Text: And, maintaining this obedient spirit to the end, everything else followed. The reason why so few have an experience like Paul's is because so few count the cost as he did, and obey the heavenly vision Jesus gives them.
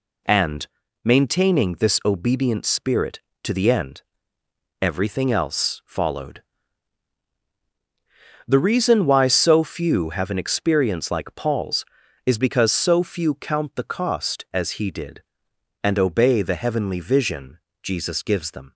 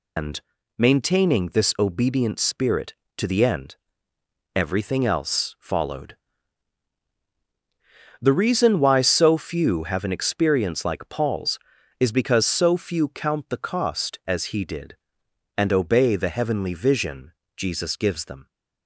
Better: first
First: pauses between "vision" and "Jesus"; slight; at 17.5 s; 0.24 s long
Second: loses the start of "And"; at 0.1 s; 170 ms // pauses between "vision" and "Jesus"; slight; at 17.3 s; 0.24 s long

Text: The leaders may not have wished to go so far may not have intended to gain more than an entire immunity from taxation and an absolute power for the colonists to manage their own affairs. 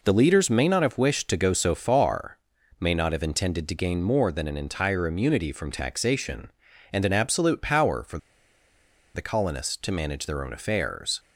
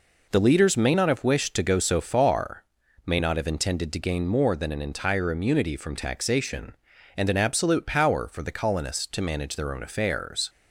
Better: second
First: pauses between "far" and "may"; noticeable; at 2.3 s; 0.46 s long // pauses between "for" and "the"; noticeable; at 8.1 s; 0.97 s long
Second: pauses between "far" and "may"; noticeable; at 2.6 s; 0.46 s long

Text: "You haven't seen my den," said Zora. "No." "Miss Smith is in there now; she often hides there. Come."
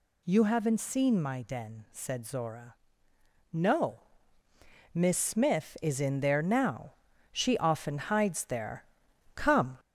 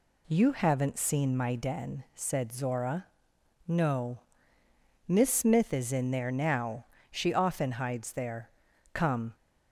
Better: second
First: gets louder; slight; throughout; 3 dB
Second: none

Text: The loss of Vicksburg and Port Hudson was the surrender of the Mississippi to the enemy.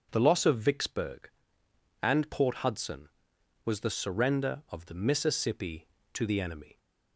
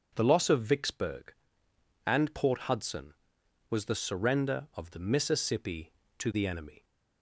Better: neither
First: starts louder than the rest; until 1.1 s; 6.5 dB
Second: starts louder than the rest; until 1.1 s; 6.5 dB

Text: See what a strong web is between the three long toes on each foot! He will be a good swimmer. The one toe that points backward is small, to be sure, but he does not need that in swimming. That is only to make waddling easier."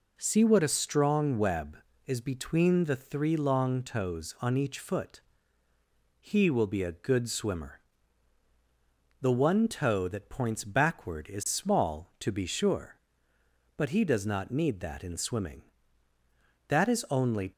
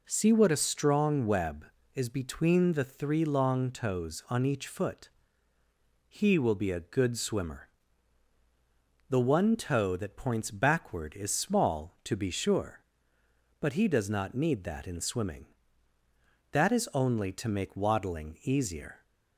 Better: second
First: stops before "to make waddling easier"; at 17.5 s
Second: none

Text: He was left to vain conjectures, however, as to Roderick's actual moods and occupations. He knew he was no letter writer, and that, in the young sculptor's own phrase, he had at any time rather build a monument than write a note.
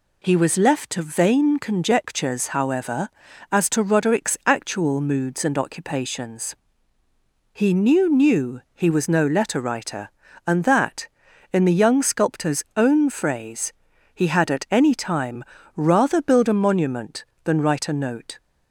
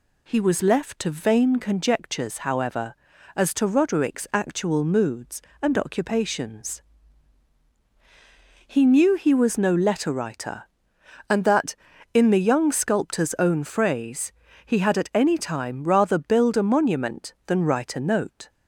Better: second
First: says "knew" twice; at 8.0 s // pauses between "time" and "rather"; slight; at 15.4 s; 0.34 s long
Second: none

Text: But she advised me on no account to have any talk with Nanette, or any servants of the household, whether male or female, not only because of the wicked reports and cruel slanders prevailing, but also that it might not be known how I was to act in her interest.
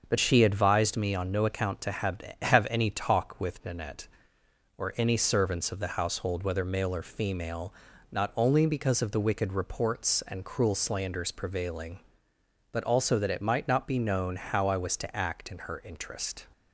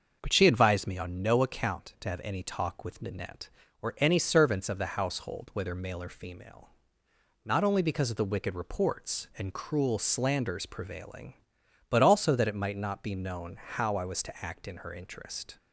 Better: second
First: starts louder than the rest; until 1.0 s; 6.5 dB // says "have" twice; at 2.4 s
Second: starts louder than the rest; until 1.2 s; 6.5 dB

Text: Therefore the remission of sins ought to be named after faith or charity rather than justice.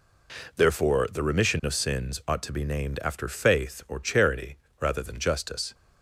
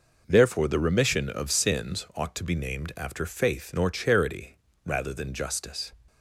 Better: first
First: pauses between "charity" and "rather"; slight; at 4.5 s; 0.24 s long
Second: says "nor" for "or"; at 3.7 s // pauses between "charity" and "rather"; slight; at 4.5 s; 0.28 s long

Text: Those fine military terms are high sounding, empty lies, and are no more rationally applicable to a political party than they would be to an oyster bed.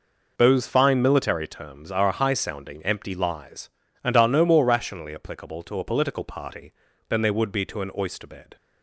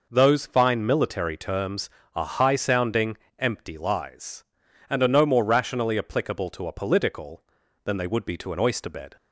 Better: first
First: none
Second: skips "party"; at 7.6 s

